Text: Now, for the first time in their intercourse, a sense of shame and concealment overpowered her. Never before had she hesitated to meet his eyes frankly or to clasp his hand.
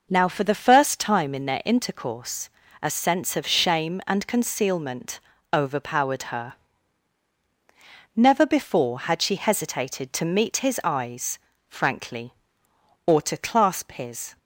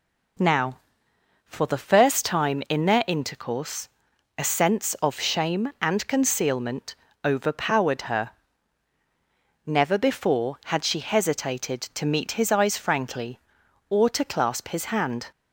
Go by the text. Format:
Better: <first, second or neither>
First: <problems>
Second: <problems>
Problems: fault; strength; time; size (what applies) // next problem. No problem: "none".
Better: second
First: pauses between "concealment" and "overpowered"; slight; at 5.1 s; 0.32 s long // pauses between "eyes" and "frankly"; slight; at 11.3 s; 0.30 s long // stops before "hand"; at 14.3 s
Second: pauses between "concealment" and "overpowered"; slight; at 6.9 s; 0.30 s long